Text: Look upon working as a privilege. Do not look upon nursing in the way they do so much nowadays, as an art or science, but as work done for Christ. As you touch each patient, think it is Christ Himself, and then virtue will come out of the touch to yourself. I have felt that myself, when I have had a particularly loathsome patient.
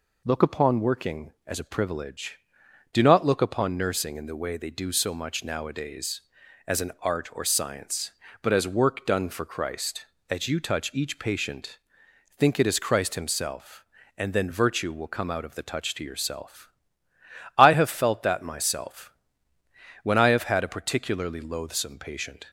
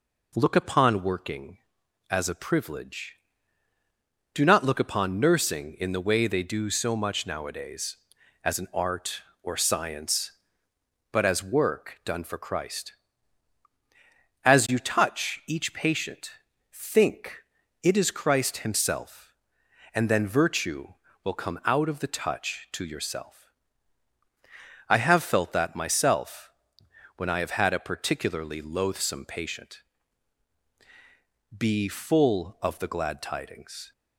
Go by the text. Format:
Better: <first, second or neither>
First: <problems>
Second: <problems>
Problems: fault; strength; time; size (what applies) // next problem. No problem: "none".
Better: first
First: none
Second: pauses between "think" and "it"; at 17.3 s; 0.44 s long // goes on to say "Be full of the Glad Tidings"; strong; from 31.5 s on; 2.3 s long